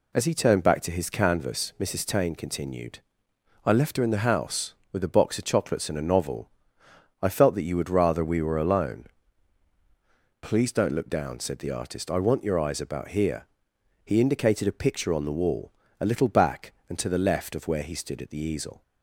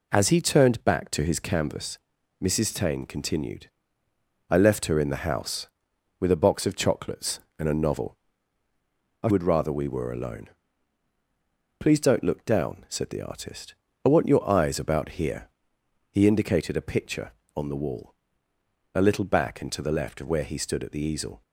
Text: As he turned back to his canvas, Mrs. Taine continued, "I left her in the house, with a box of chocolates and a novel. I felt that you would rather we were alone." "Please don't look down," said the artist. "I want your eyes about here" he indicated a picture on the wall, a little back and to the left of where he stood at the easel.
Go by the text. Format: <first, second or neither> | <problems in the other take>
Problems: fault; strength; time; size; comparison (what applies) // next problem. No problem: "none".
first | skips "felt that you"; at 9.2 s // pauses between "here" and "he"; noticeable; at 15.4 s; 0.64 s long; noticeable in the first